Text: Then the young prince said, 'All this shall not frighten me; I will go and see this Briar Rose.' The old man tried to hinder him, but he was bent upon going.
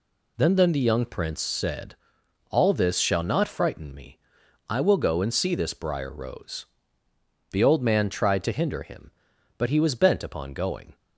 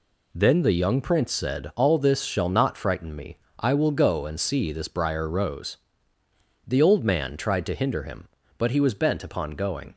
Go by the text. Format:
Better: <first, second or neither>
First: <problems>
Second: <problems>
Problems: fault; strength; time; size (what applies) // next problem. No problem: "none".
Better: second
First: says "Then" twice; at 0.5 s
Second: none